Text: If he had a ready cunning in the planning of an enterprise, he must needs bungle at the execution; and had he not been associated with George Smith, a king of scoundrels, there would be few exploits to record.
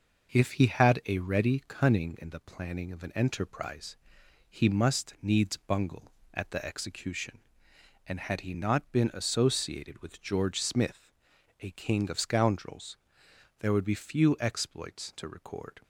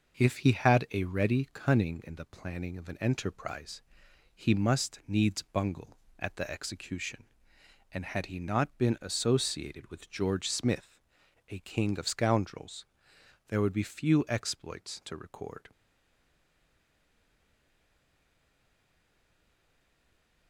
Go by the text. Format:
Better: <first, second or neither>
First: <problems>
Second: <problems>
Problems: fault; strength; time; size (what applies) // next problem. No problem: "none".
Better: first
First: none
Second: stays silent after the last word; strong; from 15.7 s on; 4.7 s long